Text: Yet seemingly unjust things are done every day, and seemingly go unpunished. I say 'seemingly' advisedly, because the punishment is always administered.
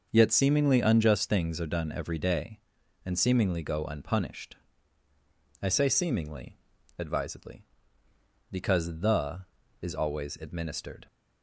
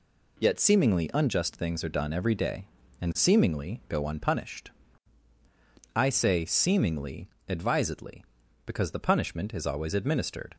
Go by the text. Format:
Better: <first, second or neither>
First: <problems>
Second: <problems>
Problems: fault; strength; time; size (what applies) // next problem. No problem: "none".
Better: second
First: starts louder than the rest; noticeable; until 1.1 s; 6 dB // pauses between "seemingly" and "advisedly"; at 6.5 s; 0.40 s long // skips "punishment"; at 9.6 s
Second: pauses between "seemingly" and "advisedly"; slight; at 7.2 s; 0.22 s long